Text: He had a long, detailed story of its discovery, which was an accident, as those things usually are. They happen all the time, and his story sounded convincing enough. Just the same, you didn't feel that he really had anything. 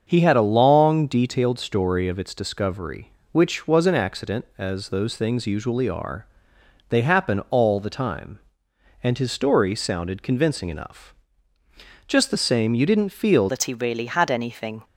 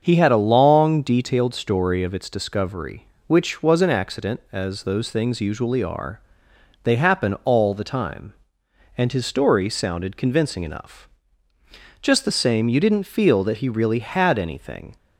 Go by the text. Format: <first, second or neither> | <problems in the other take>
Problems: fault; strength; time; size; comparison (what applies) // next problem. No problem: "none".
second | starts louder than the rest; until 1.0 s; 6.5 dB; also in the second // changes voice at "that"; from 13.4 s on; 1.4 s long